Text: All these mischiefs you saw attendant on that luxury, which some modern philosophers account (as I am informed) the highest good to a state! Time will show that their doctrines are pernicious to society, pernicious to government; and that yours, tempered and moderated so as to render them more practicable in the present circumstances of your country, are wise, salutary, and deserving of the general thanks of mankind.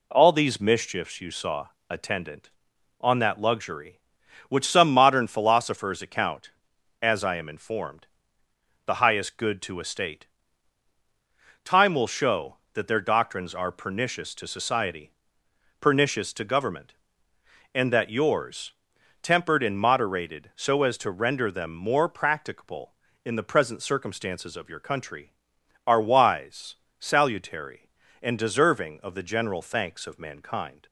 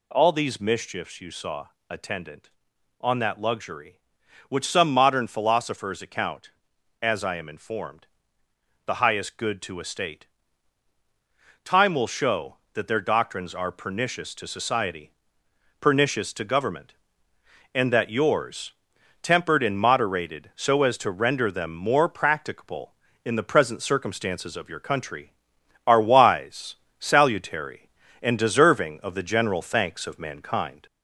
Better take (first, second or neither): first